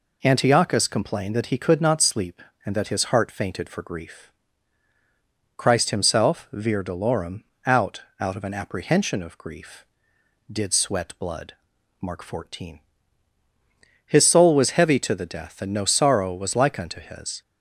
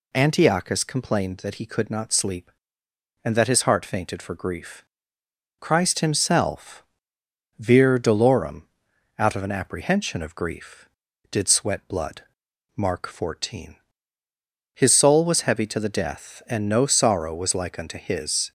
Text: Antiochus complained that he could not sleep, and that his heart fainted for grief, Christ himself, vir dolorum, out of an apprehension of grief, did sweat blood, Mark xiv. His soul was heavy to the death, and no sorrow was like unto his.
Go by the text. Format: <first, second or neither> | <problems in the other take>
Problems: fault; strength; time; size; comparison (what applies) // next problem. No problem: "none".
second | says "out" twice; at 8.1 s